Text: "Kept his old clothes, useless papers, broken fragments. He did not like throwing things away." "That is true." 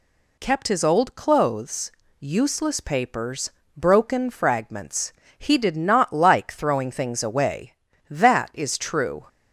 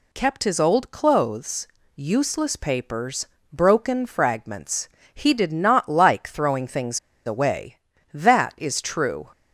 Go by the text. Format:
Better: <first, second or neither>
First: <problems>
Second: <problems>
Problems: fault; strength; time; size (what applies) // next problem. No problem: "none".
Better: first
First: none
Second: pauses between "things" and "away"; slight; at 6.9 s; 0.27 s long